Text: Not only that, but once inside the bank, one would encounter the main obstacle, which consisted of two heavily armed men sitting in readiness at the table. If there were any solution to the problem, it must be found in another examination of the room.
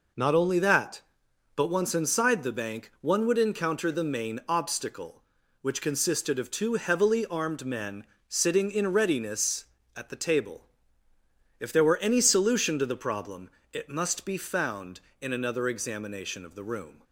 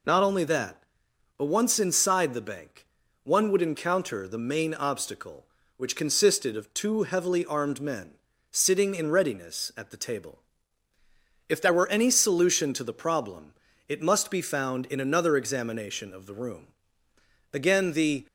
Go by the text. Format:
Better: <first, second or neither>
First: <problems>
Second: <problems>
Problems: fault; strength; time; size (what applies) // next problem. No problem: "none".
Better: first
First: pauses between "men" and "sitting"; slight; at 8.0 s; 0.24 s long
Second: pauses between "men" and "sitting"; at 8.1 s; 0.38 s long // goes on to say "Again the"; noticeable; from 17.5 s on; 0.74 s long